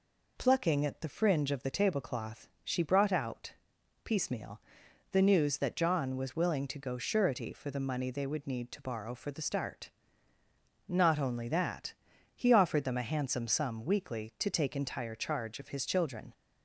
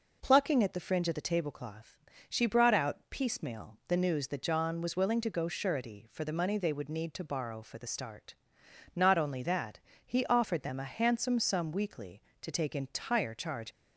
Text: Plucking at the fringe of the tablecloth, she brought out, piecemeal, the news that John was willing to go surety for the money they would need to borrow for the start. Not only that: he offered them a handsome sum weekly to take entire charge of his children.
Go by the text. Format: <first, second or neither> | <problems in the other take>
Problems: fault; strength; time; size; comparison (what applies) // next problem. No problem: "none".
first | stops before "of his children"; at 13.7 s